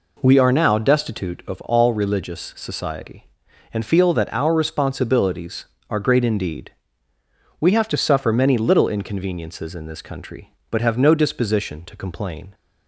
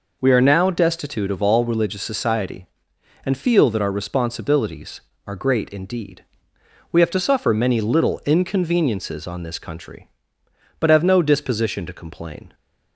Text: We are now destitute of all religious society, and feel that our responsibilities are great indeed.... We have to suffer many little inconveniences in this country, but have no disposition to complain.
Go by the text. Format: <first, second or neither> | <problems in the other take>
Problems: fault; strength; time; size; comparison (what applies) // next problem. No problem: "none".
first | says "on" for "in"; at 9.2 s